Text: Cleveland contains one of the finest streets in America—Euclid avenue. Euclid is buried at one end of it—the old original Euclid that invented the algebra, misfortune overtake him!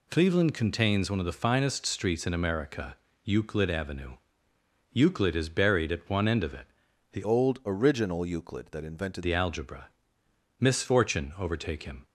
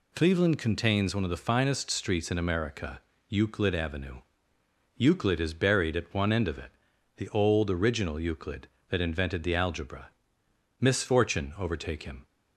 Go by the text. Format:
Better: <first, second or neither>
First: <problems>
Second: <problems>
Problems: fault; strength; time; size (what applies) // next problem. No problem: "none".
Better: second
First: changes voice from "old" to "invented"; from 7.2 to 9.2 s; 2.0 s long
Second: none